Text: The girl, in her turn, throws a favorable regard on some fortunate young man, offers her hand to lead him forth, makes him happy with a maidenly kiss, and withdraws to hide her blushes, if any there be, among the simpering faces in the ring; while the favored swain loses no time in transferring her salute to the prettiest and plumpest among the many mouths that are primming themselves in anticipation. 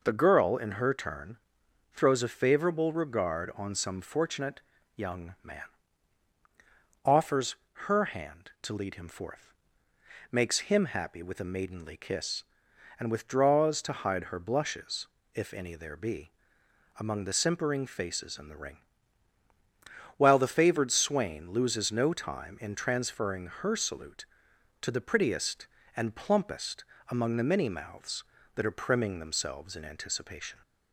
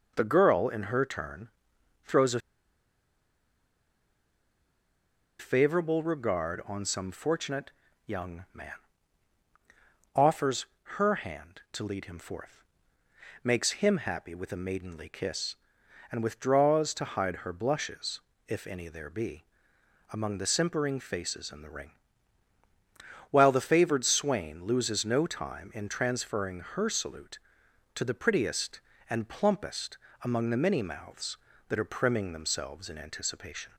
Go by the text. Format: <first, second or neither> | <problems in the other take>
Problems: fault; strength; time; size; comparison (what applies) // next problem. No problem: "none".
first | pauses between "a" and "favorable"; strong; at 2.3 s; 3.0 s long // pauses between "fortunate" and "young"; slight; at 7.6 s; 0.36 s long; slight in the first // pauses between "offers" and "her"; slight; at 10.6 s; 0.32 s long; slight in the first // pauses between "plumpest" and "among"; slight; at 29.9 s; 0.24 s long; slight in the first